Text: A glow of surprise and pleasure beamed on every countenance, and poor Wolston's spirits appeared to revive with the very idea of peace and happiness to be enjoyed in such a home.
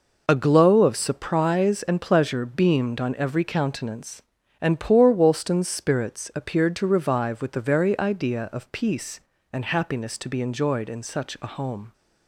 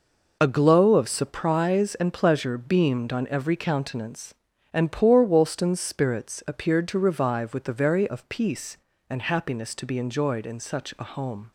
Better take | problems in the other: first | skips "idea"; at 8.0 s

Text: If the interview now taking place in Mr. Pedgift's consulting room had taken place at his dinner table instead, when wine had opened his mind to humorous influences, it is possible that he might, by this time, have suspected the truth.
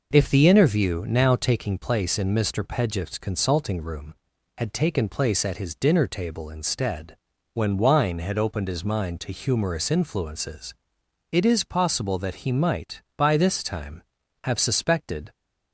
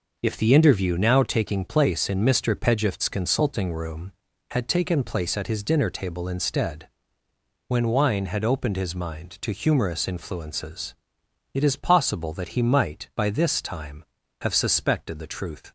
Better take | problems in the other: second | stops before "the truth"; at 15.3 s

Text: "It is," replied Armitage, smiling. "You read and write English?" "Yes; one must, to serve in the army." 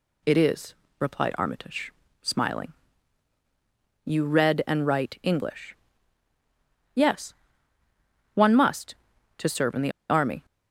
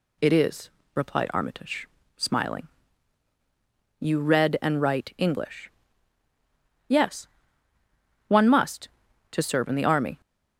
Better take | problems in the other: second | pauses between "the" and "army"; slight; at 9.9 s; 0.18 s long

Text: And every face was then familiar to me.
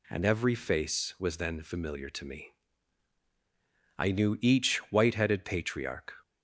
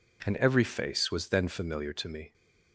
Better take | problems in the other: second | goes on to say "I knew each white headed patriarch"; strong; from 3.9 s on; 2.1 s long

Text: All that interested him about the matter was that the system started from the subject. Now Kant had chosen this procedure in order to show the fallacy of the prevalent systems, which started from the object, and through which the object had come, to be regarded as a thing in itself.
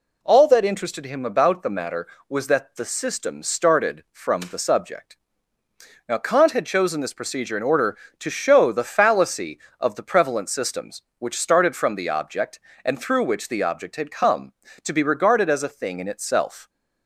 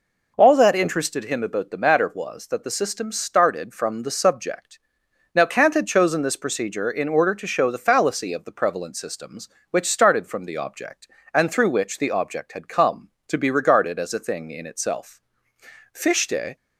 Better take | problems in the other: first | goes on to say "Fichte"; noticeable; from 15.9 s on; 0.62 s long

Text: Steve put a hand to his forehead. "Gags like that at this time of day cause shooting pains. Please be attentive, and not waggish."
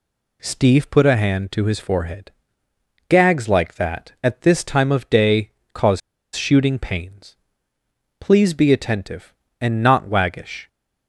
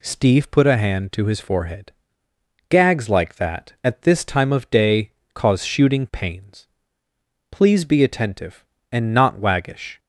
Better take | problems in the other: second | pauses between "day" and "cause"; slight; at 5.5 s; 0.24 s long; slight in the second // pauses between "cause" and "shooting"; slight; at 6.0 s; 0.35 s long

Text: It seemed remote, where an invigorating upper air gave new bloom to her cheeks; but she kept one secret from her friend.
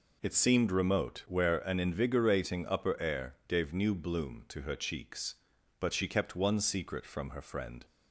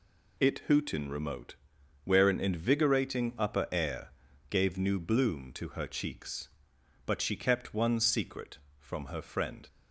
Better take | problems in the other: first | says "hootin" for "seemed"; at 0.6 s // pauses between "air" and "gave"; at 4.1 s; 0.40 s long

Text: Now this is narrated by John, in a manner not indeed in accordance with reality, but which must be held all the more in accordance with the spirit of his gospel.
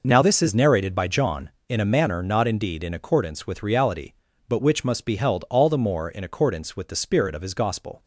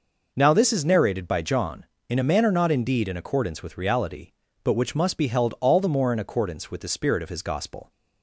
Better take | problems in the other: neither | none

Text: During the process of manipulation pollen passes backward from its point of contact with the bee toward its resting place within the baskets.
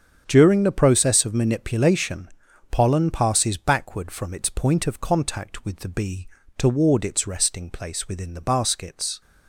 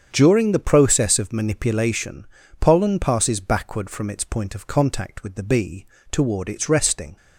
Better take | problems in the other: first | starts louder than the rest; strong; until 1.1 s; 7.5 dB; strong in the first // pauses between "manipulation" and "pollen"; slight; at 2.2 s; 0.34 s long; also in the first // pauses between "bee" and "toward"; slight; at 5.8 s; 0.26 s long; slight in the first // stops before "place within the baskets"; at 7.1 s

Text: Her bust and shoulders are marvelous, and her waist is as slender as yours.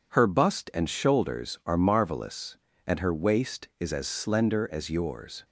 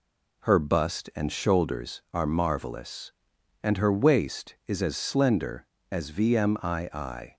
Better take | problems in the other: first | says "vmii" for "yours"; at 6.1 s

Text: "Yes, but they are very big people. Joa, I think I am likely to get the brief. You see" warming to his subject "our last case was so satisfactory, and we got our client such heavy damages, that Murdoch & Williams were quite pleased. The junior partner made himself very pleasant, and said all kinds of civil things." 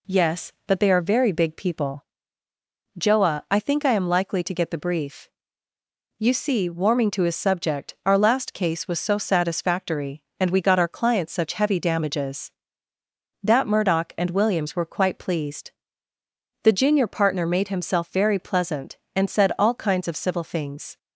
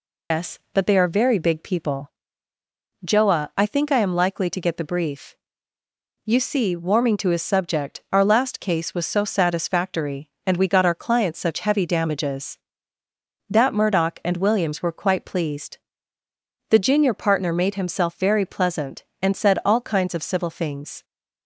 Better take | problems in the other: first | loses the start of "Yes"; at 0.3 s; 180 ms

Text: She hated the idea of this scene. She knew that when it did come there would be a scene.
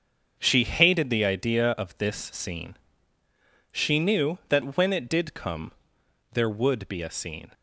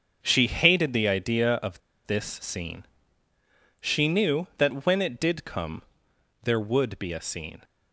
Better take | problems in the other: first | starts louder than the rest; until 1.2 s; 6.5 dB; also in the first // pauses between "of" and "this"; slight; at 1.8 s; 0.25 s long // pauses between "come" and "there"; noticeable; at 5.8 s; 0.62 s long; noticeable in the first

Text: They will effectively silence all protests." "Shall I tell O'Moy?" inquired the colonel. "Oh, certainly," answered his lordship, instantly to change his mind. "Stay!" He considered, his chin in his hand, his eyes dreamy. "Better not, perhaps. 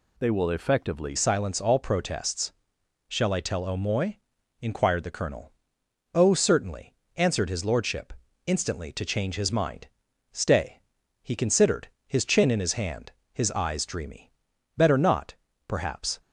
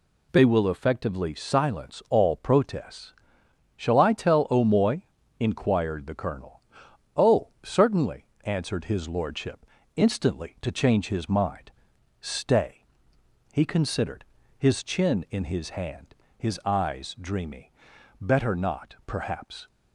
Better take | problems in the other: second | changes voice at "silence"; from 1.1 s on; 15.0 s long

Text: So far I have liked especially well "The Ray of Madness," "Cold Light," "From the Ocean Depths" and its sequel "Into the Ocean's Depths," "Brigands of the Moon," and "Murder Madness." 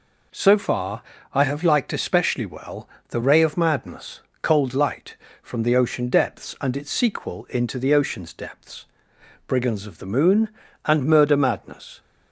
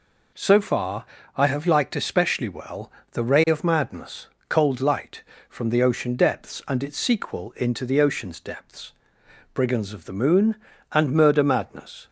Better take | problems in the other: neither | pauses between "far" and "I"; slight; the same in both // pauses between "well" and "The"; slight; the same in both

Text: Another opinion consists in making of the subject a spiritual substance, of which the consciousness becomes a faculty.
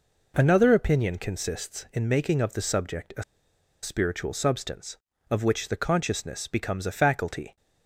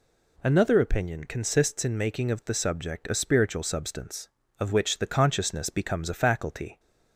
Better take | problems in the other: second | pauses between "a" and "spiritual"; noticeable; at 3.2 s; 0.59 s long

